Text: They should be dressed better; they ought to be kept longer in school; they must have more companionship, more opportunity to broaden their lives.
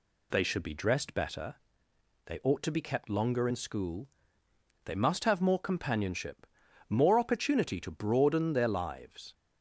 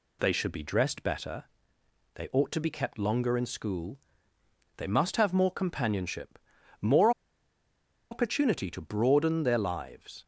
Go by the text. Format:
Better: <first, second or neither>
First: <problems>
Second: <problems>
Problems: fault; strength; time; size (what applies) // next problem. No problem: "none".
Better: first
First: none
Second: pauses between "more" and "opportunity"; at 7.1 s; 1.0 s long